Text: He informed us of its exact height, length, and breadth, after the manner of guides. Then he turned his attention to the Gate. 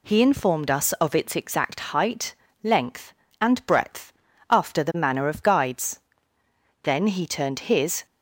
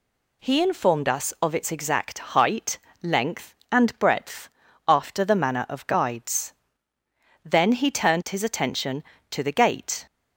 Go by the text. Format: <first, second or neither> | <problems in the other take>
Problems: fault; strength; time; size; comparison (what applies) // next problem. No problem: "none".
second | stops before "attention to the Gate"; at 8.0 s